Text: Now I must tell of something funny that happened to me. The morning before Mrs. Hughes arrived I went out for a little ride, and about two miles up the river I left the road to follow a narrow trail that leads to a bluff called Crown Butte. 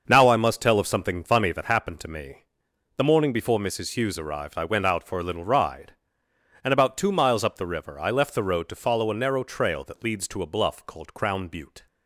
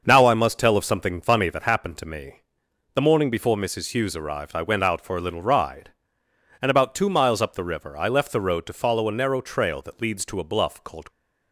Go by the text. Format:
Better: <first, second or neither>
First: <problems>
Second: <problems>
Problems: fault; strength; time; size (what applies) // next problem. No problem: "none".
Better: first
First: starts louder than the rest; until 1.0 s; 6.5 dB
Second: starts louder than the rest; until 1.0 s; 6.5 dB // stops before "Crown Butte"; at 11.0 s